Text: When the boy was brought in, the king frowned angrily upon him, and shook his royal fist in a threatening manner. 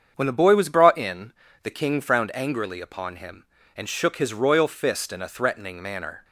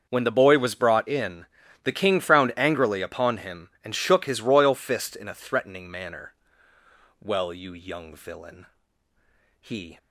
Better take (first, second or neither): first